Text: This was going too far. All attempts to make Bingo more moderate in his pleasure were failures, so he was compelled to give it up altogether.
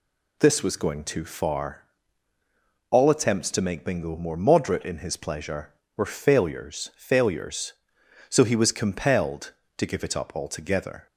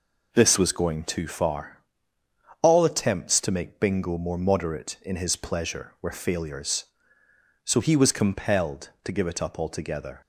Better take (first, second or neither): second